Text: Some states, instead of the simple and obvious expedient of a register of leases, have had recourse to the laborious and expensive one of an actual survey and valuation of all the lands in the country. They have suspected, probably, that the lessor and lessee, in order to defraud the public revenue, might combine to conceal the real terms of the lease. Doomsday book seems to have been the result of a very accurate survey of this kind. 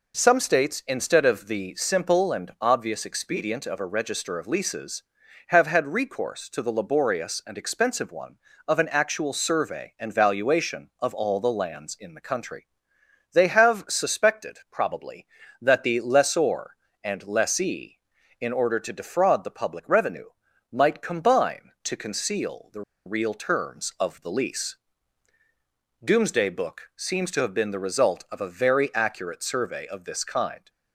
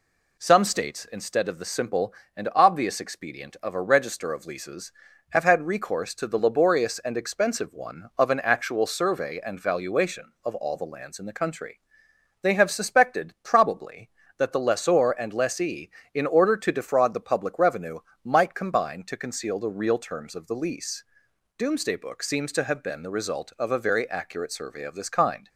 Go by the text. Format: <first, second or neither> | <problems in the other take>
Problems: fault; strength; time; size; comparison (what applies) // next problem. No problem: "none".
second | pauses between "the" and "real"; slight; at 22.8 s; 0.24 s long